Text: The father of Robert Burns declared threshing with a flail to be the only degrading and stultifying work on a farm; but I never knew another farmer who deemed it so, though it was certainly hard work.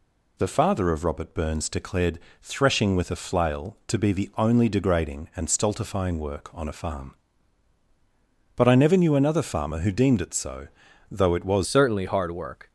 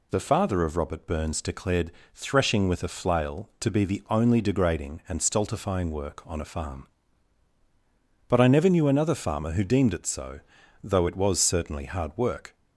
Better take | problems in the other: second | pauses between "declared" and "threshing"; slight; at 2.1 s; 0.24 s long; slight in the second // changes voice at "certainly"; from 11.6 s on; 1.1 s long

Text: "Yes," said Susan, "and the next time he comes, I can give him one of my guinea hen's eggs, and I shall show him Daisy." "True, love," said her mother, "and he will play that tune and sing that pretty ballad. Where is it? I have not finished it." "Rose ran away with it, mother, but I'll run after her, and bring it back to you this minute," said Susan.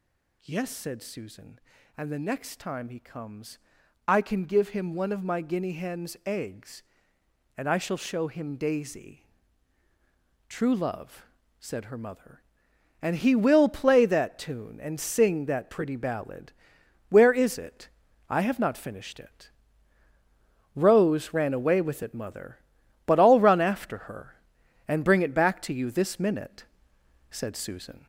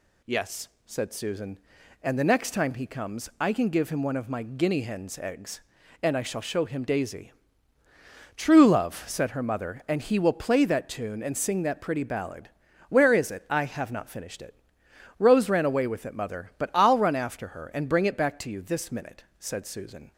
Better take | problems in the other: second | gets louder; noticeable; throughout; 5 dB

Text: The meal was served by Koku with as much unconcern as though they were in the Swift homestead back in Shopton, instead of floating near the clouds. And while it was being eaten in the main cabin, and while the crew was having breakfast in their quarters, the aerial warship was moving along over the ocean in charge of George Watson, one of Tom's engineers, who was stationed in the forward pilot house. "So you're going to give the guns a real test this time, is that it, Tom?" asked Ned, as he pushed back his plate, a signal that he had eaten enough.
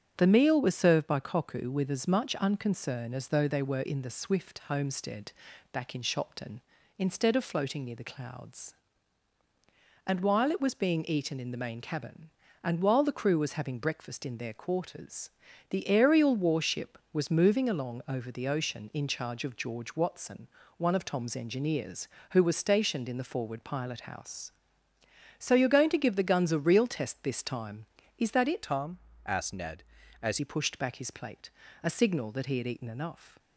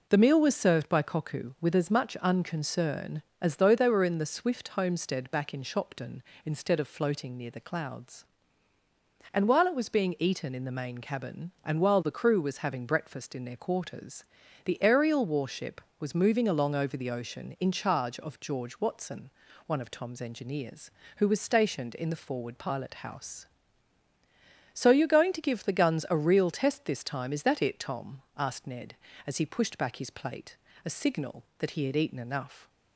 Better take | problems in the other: second | starts louder than the rest; strong; until 1.1 s; 7.5 dB // pauses between "homestead" and "back"; at 5.3 s; 0.40 s long // changes voice from "Tom" to "as"; from 28.6 to 30.3 s; 1.7 s long

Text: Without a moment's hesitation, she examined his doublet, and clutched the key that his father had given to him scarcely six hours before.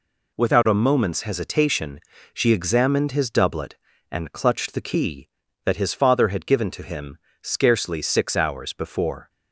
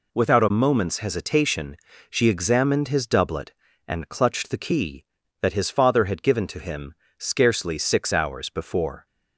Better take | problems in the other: neither | pauses between "him" and "scarcely"; slight; the same in both

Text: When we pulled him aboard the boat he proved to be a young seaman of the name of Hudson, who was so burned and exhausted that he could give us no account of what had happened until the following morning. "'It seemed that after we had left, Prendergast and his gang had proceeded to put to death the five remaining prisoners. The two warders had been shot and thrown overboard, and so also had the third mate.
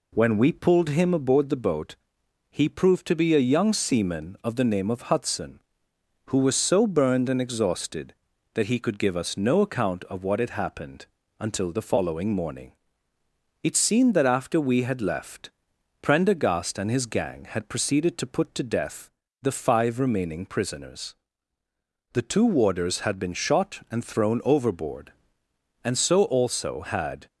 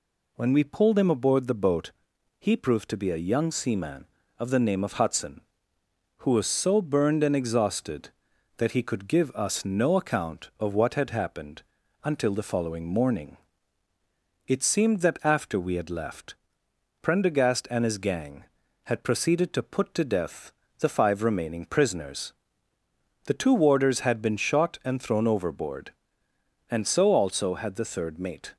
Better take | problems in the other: second | pauses between "boat" and "he"; noticeable; at 1.9 s; 0.56 s long; noticeable in the second // pauses between "happened" and "until"; slight; at 11.0 s; 0.32 s long; also in the second // pauses between "death" and "the"; slight; at 19.0 s; 0.32 s long; slight in the second // stops before "the third mate"; at 27.2 s

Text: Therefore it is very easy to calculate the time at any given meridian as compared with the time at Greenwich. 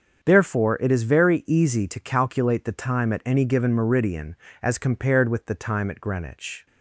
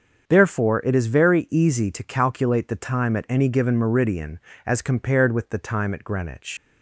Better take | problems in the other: first | starts louder than the rest; until 1.2 s; 6.5 dB; also in the first // leaves "Greenwich" unfinished; at 6.5 s; 120 ms

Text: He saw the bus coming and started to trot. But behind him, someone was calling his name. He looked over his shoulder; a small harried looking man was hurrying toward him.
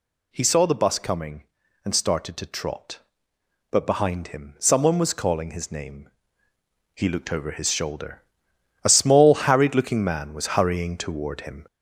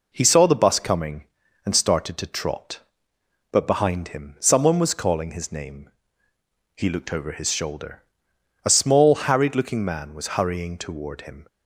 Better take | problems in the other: second | gets louder; throughout; 3.5 dB

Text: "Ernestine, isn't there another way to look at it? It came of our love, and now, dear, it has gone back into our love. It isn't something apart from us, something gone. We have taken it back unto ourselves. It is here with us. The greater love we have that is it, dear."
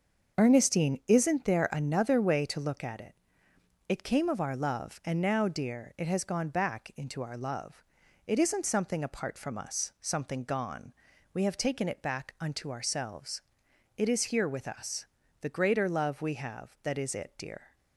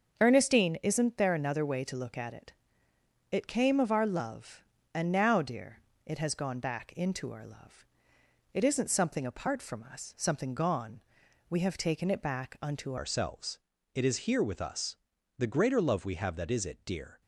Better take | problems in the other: first | starts louder than the rest; until 1.2 s; 6.5 dB; also in the first // changes voice at "ourselves"; from 12.9 s on; 4.3 s long

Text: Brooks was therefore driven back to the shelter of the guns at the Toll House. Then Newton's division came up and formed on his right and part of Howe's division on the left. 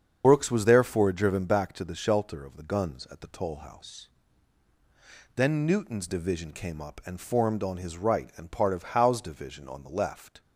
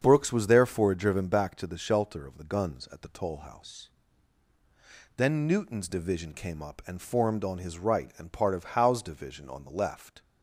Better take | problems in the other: second | loses the start of "Brooks"; at 0.2 s; 45 ms // starts louder than the rest; strong; until 1.2 s; 7.5 dB; strong in the second

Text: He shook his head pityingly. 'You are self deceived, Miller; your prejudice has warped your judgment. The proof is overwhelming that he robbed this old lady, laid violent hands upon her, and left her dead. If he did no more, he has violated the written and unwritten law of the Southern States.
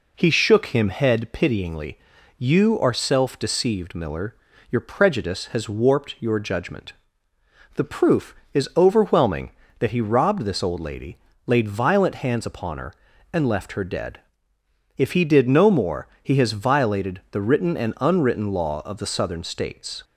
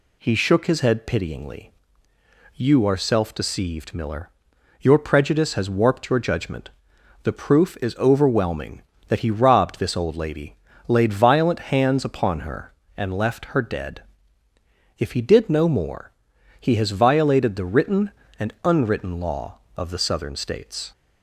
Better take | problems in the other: second | says "him" for "his"; at 0.6 s

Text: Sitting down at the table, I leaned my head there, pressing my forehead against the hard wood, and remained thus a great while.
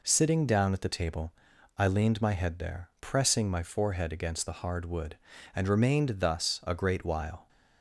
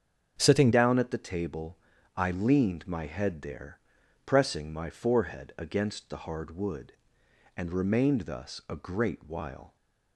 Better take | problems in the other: first | starts louder than the rest; strong; until 1.4 s; 7.5 dB // changes voice at "down"; from 0.7 s on; 9.0 s long

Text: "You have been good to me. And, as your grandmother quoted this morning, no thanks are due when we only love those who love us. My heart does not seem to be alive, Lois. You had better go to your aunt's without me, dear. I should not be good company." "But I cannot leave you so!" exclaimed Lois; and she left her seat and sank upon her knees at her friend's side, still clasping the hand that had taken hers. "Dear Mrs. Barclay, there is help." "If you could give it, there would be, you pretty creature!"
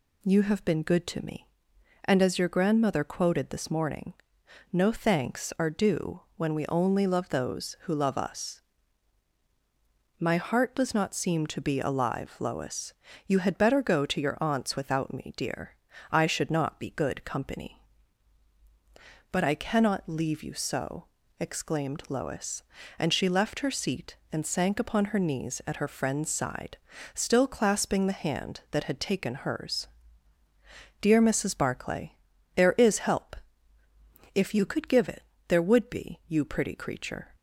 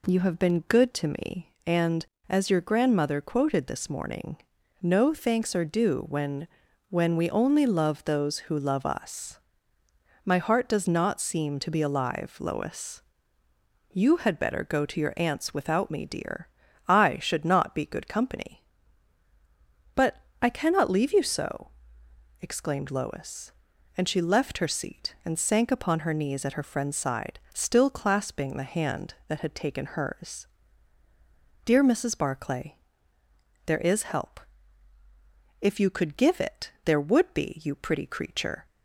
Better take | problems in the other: first | says "when" twice; at 6.9 s // pauses between "But" and "I"; slight; at 20.2 s; 0.20 s long

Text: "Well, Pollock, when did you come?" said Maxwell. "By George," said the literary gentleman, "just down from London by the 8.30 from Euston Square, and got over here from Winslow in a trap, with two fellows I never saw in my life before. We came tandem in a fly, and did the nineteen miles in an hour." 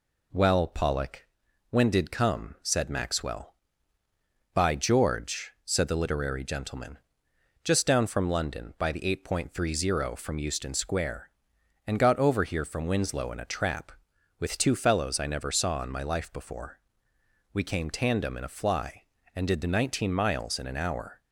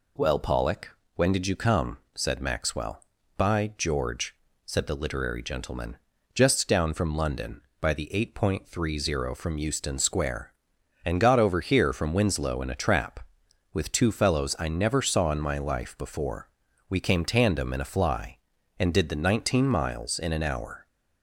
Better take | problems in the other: second | skips "you"; at 2.1 s

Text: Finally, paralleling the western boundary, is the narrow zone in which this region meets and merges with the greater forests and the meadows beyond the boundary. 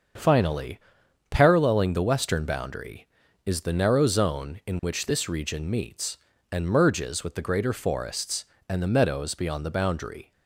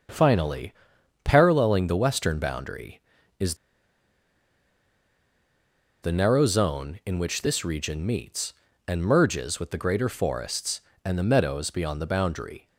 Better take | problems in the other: first | starts louder than the rest; until 1.6 s; 7 dB; also in the first // pauses between "is" and "the"; strong; at 3.5 s; 2.4 s long

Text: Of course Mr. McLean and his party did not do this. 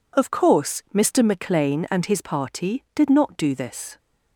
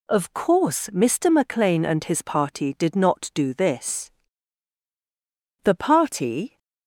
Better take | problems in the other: first | goes on to say "The party"; noticeable; from 5.6 s on; 0.94 s long

